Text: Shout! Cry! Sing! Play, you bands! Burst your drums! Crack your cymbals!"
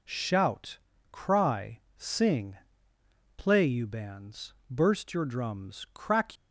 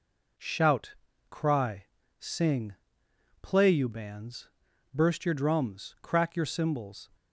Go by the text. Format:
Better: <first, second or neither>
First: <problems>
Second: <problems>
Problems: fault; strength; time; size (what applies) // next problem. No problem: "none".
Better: second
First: stops before "your cymbals"; at 6.3 s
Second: none